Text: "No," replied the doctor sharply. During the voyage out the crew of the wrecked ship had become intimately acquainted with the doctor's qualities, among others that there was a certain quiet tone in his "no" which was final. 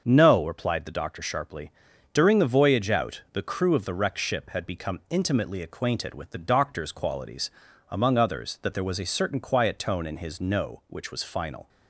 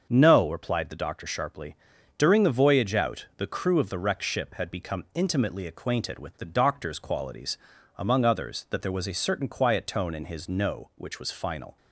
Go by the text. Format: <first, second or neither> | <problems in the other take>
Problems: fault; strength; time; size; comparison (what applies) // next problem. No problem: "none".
neither | starts louder than the rest; the same in both